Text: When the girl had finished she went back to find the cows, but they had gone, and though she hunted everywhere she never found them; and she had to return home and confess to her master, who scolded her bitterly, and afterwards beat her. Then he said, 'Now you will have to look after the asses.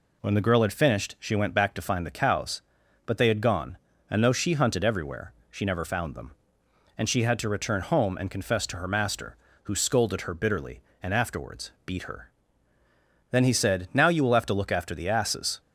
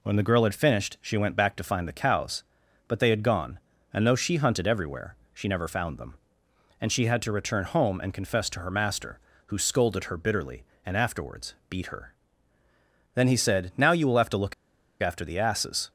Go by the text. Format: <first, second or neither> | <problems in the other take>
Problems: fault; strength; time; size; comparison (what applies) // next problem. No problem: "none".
first | pauses between "everywhere" and "she"; slight; at 5.1 s; 0.18 s long; slight in the first // pauses between "afterwards" and "beat"; slight; at 11.5 s; 0.16 s long; slight in the first // pauses between "look" and "after"; noticeable; at 14.5 s; 0.48 s long